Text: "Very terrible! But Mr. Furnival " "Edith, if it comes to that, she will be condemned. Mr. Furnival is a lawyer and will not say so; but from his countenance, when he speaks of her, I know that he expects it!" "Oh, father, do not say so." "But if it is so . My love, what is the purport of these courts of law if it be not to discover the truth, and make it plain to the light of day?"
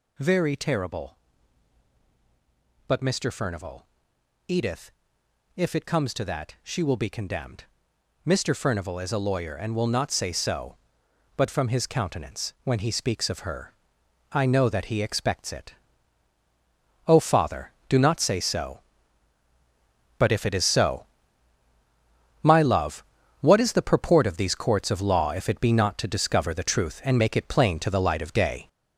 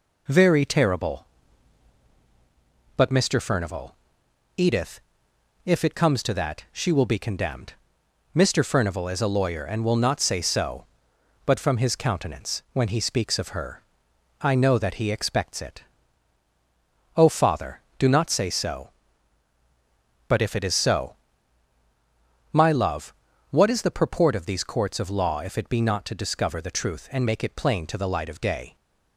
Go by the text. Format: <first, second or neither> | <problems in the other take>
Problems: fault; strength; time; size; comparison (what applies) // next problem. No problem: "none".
second | gets louder; strong; throughout; 8 dB